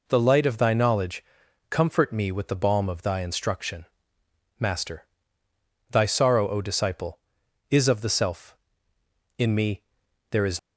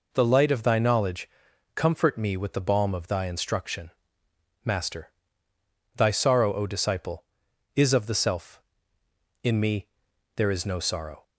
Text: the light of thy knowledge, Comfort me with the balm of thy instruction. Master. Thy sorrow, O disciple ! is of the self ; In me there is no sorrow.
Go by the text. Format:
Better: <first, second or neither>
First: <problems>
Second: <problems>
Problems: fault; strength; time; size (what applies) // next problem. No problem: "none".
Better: second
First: pauses between "me" and "there"; noticeable; at 9.8 s; 0.48 s long // stops before "no sorrow"; at 10.5 s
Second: pauses between "me" and "there"; noticeable; at 9.8 s; 0.48 s long